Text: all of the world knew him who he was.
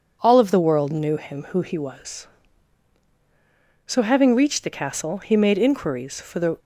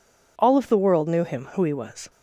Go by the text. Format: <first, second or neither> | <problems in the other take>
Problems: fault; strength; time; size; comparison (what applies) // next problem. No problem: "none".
second | goes on to say "So having reached the castle he made inquiries for the"; strong; from 3.8 s on; 2.7 s long